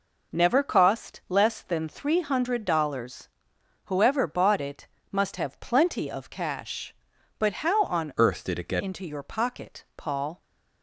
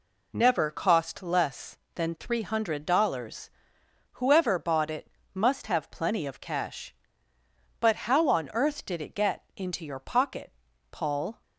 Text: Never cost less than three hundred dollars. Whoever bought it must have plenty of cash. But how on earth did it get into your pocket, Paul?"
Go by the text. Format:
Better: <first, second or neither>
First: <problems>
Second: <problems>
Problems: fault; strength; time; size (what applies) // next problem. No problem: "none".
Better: second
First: pauses between "it" and "must"; slight; at 4.8 s; 0.24 s long // changes voice from "earth" to "get"; from 8.1 to 8.8 s; 0.7 s long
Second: pauses between "it" and "must"; slight; at 5.0 s; 0.24 s long